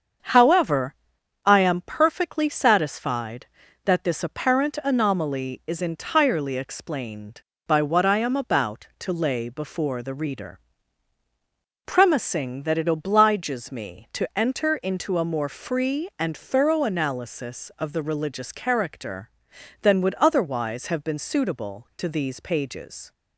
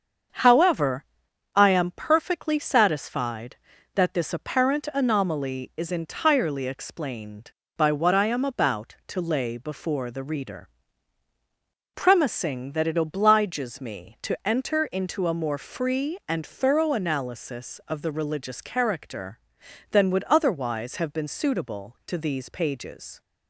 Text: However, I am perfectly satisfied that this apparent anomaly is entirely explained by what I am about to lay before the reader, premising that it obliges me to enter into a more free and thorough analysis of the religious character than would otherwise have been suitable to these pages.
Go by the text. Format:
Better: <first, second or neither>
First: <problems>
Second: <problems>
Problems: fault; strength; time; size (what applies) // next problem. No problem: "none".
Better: neither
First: starts louder than the rest; strong; until 1.7 s; 7 dB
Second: starts louder than the rest; strong; until 1.8 s; 7 dB